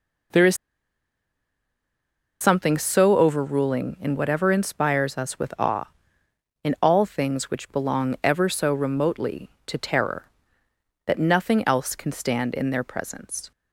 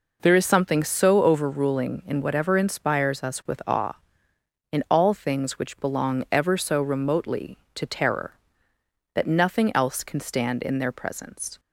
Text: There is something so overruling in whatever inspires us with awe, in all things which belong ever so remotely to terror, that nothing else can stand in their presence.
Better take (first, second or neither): second